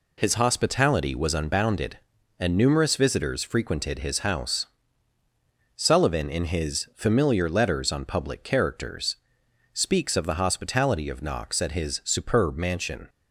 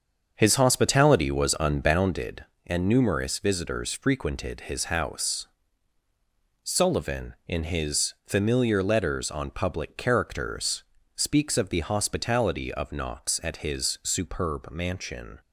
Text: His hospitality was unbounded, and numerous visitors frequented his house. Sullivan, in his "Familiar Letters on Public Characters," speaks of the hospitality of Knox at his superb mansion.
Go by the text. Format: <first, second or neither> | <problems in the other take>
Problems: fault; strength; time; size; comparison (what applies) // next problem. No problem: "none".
first | starts louder than the rest; strong; until 2.2 s; 7 dB